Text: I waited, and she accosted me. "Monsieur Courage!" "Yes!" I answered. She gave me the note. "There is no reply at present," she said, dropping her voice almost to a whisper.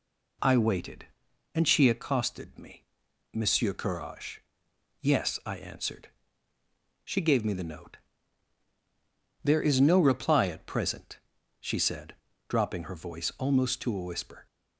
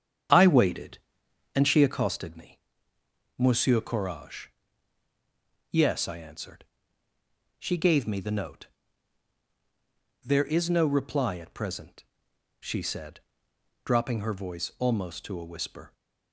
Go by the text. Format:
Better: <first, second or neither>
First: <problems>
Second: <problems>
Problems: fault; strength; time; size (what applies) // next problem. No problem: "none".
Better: first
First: none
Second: starts louder than the rest; strong; until 2.2 s; 8 dB